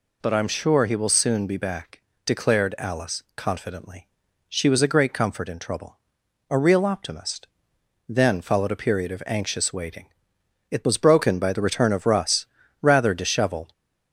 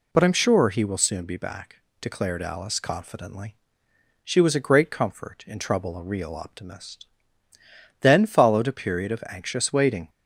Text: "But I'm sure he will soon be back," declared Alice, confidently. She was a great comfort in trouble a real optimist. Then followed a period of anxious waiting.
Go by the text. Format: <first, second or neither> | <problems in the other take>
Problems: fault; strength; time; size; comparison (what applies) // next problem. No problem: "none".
second | pauses between "trouble" and "a"; noticeable; at 5.9 s; 0.56 s long // goes on to say "It was broken by the return of Russ rather disheveled"; strong; from 10.7 s on; 3.0 s long